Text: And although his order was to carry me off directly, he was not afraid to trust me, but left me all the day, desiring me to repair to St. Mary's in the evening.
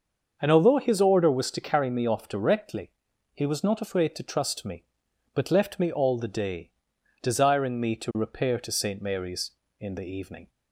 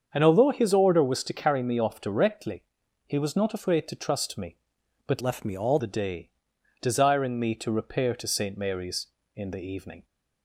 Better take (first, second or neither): first